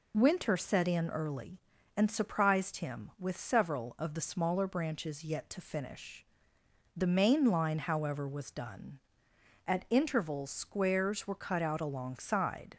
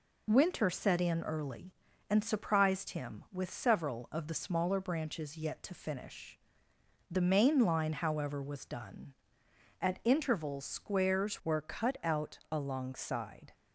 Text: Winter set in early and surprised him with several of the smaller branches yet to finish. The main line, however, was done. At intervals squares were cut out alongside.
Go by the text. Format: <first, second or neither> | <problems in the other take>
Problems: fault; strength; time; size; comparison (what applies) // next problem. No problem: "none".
first | changes voice at "were"; from 11.4 s on; 2.1 s long